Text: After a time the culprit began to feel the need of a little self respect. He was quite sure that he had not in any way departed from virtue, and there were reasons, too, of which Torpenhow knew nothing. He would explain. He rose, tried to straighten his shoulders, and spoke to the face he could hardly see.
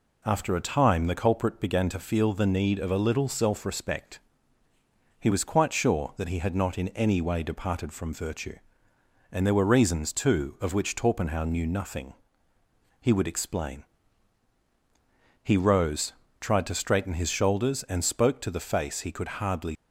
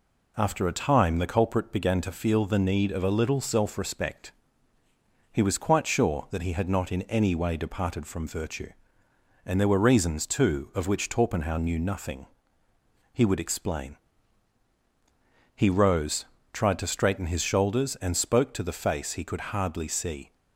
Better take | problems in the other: second | stops before "see"; at 19.7 s

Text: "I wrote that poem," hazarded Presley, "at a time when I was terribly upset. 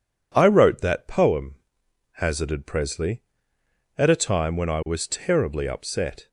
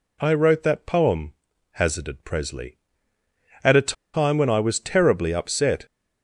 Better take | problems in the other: first | pauses between "a" and "time"; slight; at 3.9 s; 0.21 s long

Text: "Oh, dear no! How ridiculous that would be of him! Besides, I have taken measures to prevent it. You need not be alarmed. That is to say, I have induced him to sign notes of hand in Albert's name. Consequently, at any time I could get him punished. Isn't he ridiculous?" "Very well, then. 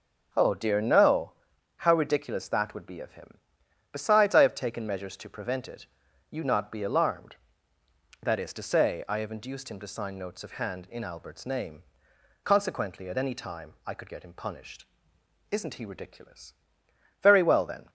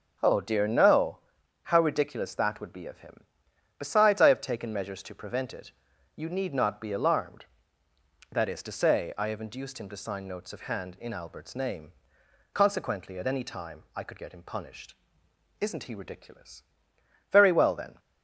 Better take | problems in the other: second | skips "need"; at 6.4 s

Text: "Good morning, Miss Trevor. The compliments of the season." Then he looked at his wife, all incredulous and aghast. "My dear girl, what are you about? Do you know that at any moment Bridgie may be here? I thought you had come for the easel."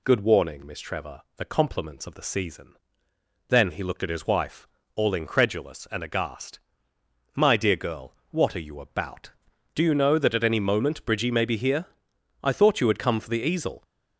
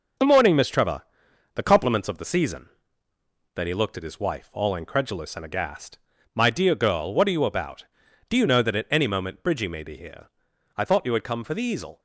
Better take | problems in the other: second | says "warning" for "morning"; at 0.2 s

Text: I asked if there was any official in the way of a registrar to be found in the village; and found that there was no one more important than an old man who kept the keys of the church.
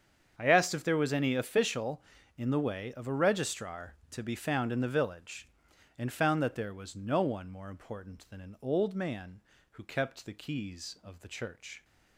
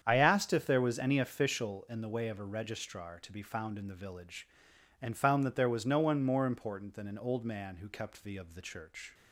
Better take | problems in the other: first | starts louder than the rest; strong; until 1.0 s; 8 dB; strong in the first // skips "keys"; at 8.3 s

